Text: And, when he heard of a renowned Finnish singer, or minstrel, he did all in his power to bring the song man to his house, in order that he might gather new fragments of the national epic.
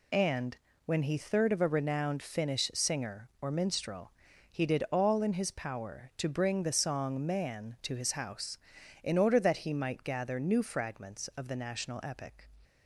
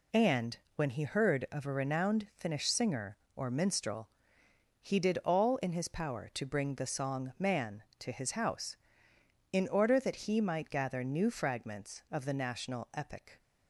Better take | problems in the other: second | says "third" for "heard"; at 1.1 s

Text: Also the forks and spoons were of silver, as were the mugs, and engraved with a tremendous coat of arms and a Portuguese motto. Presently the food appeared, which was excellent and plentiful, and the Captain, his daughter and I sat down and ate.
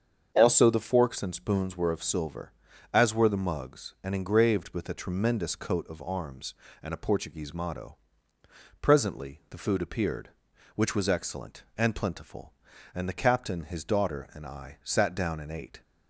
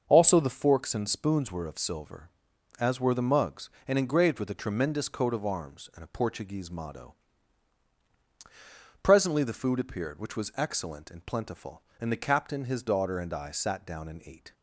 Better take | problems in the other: neither | starts louder than the rest; the same in both

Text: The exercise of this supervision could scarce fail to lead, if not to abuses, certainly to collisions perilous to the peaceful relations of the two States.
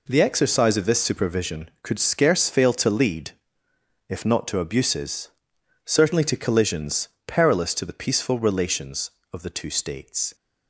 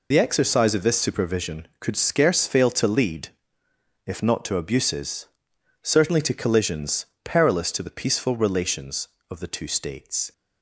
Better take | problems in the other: first | loses the start of "The"; at 0.1 s; 60 ms // pauses between "collisions" and "perilous"; slight; at 7.0 s; 0.18 s long; slight in the first

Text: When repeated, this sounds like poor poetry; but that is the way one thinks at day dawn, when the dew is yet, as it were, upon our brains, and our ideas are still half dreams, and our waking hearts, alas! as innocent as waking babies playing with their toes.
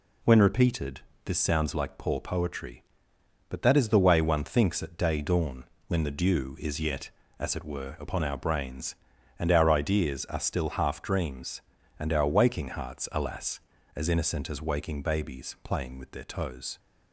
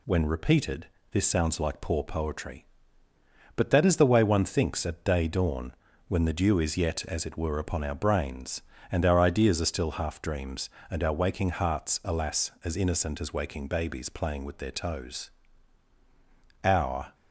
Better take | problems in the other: first | goes on to say "Our"; from 16.6 s on; 0.50 s long

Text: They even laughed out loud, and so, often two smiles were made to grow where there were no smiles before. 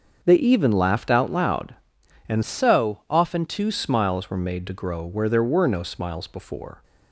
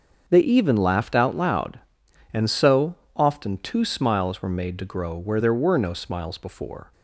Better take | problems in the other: second | starts louder than the rest; until 1.2 s; 6.5 dB; also in the second // changes voice from "so" to "two"; from 2.4 to 3.7 s; 1.3 s long

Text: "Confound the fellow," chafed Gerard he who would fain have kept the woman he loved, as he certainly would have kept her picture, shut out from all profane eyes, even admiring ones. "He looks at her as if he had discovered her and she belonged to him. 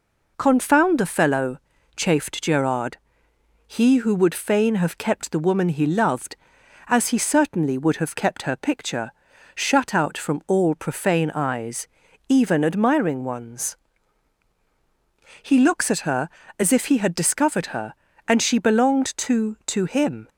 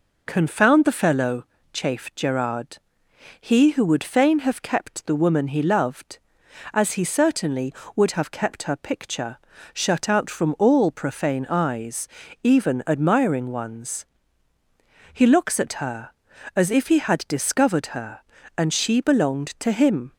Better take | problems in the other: second | pauses between "Gerard" and "he"; noticeable; at 2.9 s; 0.70 s long; noticeable in the second // says "to" twice; at 19.6 s

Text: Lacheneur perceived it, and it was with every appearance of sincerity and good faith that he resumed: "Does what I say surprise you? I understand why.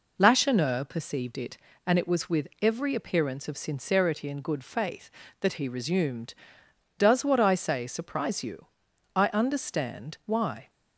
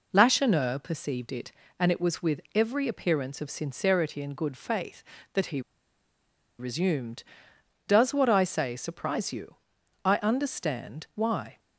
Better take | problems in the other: first | pauses between "he" and "resumed"; at 5.6 s; 0.98 s long

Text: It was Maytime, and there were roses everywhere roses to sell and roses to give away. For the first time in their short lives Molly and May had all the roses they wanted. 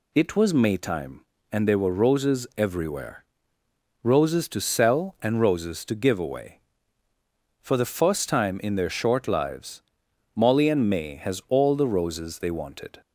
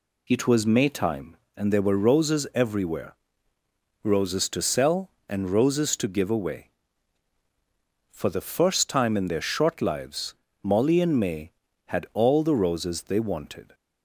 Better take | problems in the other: second | pauses between "everywhere" and "roses"; noticeable; at 3.2 s; 0.78 s long; noticeable in the second // pauses between "lives" and "Molly"; noticeable; at 9.8 s; 0.52 s long; slight in the second // says "has" for "had"; at 11.1 s

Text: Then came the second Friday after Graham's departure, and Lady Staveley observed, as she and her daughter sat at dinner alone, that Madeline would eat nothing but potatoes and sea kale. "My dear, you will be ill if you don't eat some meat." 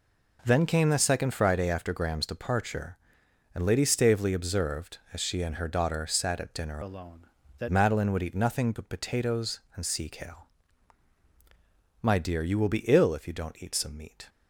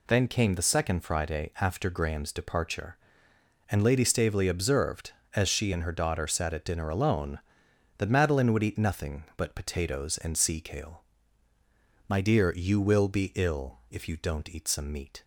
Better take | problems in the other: second | changes voice from "alone" to "that"; from 6.8 to 7.6 s; 0.8 s long

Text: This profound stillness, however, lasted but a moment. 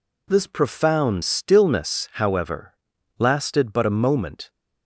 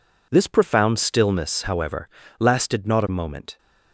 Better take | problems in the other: first | says "not" for "but"; at 2.8 s

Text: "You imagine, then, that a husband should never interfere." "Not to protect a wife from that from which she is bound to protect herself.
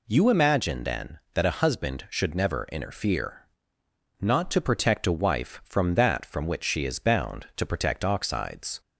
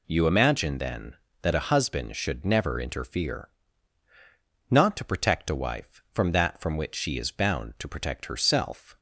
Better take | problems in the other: second | says "oxides" for "herself"; at 8.0 s

